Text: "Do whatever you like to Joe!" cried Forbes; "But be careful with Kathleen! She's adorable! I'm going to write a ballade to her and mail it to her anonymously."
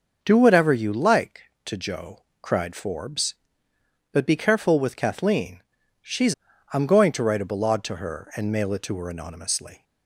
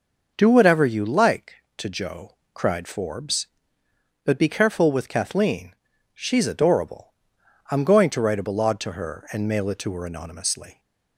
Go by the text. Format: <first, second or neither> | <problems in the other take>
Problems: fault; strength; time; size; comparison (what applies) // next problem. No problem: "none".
second | starts louder than the rest; noticeable; until 1.2 s; 6 dB // skips "adorable"; at 6.5 s